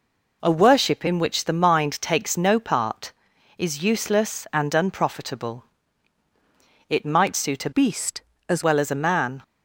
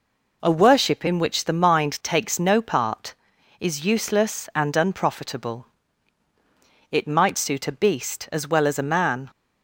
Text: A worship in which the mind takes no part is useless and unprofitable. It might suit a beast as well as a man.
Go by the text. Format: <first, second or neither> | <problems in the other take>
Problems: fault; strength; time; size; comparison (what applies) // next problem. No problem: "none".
second | changes voice from "beast" to "as"; from 7.7 to 8.6 s; 0.9 s long